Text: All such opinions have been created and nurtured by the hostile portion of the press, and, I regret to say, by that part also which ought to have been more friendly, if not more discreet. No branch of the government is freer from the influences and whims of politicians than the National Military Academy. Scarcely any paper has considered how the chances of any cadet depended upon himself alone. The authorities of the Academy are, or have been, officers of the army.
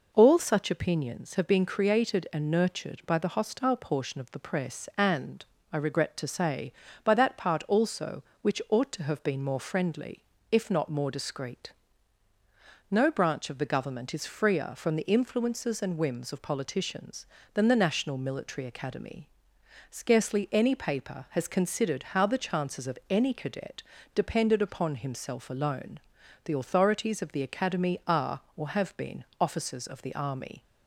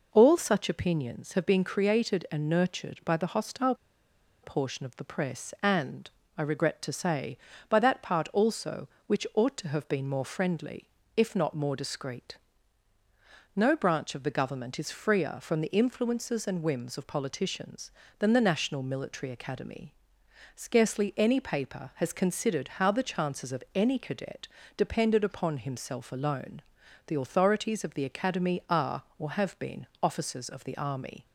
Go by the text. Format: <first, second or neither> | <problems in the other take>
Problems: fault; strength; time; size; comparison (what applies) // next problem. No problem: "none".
first | pauses between "hostile" and "portion"; noticeable; at 3.7 s; 0.68 s long // pauses between "cadet" and "depended"; slight; at 24.4 s; 0.26 s long; slight in the first